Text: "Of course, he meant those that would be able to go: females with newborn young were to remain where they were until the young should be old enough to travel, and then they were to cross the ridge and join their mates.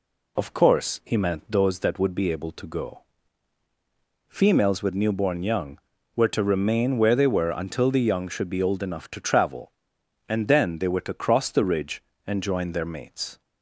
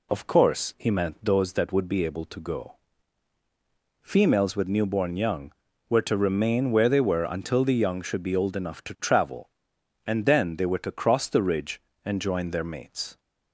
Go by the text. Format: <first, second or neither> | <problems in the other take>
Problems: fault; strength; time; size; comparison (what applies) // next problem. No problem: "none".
neither | none